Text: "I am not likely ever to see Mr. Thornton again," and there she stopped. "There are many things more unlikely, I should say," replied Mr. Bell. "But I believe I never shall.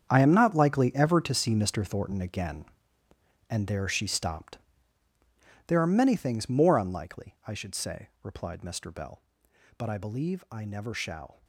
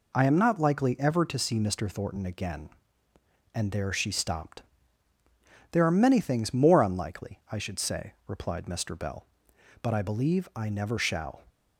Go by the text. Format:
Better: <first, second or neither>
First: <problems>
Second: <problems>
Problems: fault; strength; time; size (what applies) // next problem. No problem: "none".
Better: second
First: gets quieter; strong; throughout; 14 dB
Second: none